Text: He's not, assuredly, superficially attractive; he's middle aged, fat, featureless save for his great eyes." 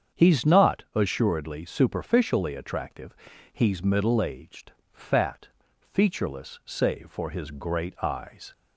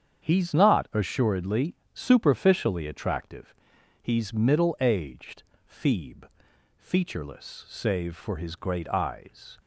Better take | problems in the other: first | starts louder than the rest; strong; until 1.2 s; 8 dB; strong in the first // says "feeb" for "fat"; at 5.6 s

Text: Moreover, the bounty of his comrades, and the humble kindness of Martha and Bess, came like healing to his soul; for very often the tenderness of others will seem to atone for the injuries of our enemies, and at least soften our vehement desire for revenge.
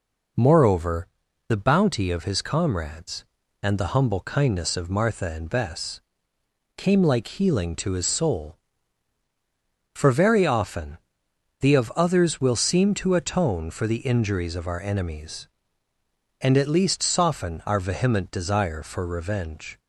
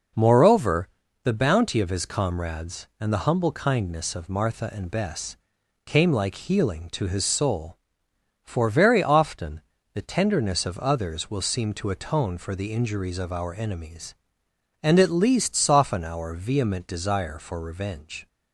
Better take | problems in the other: second | pauses between "often" and "the"; noticeable; at 10.9 s; 0.62 s long; slight in the second // skips "tenderness"; at 11.7 s

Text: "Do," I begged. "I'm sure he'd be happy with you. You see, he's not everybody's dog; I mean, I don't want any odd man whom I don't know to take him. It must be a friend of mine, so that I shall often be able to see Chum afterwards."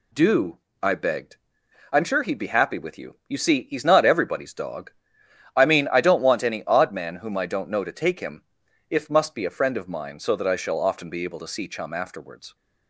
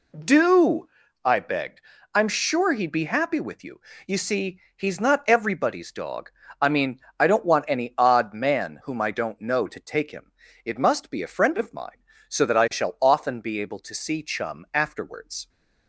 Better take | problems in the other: second | says "If" for "It"; at 8.8 s

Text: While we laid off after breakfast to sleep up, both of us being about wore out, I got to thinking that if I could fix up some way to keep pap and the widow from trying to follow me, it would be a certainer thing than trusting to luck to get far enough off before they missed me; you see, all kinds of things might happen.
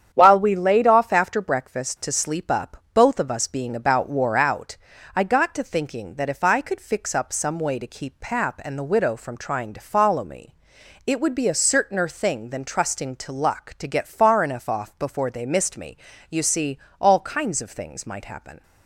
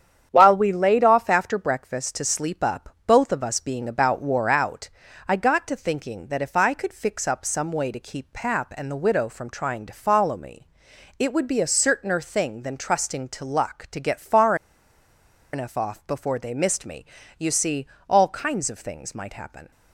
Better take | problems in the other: first | starts louder than the rest; strong; until 1.3 s; 8.5 dB; strong in the first // pauses between "far" and "enough"; at 14.5 s; 0.98 s long

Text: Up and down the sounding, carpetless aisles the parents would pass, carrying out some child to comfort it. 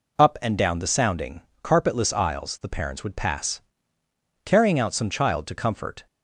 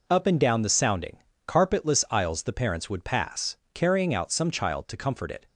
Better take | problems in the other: second | stops before "it"; at 6.0 s

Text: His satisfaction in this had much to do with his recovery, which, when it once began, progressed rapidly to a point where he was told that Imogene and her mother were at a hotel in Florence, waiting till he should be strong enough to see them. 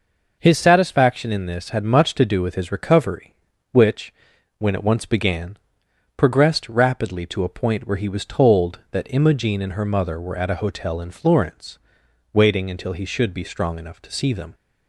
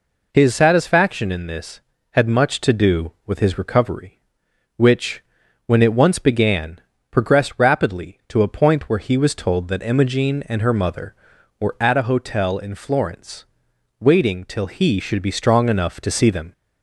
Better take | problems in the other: second | says "until" for "till"; at 12.7 s

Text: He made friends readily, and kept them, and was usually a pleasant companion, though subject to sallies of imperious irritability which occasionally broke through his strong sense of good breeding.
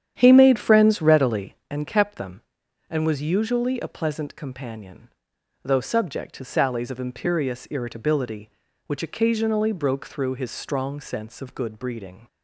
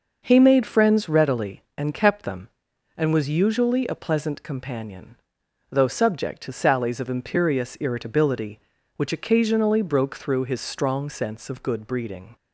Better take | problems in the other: second | starts louder than the rest; strong; until 1.8 s; 9.5 dB

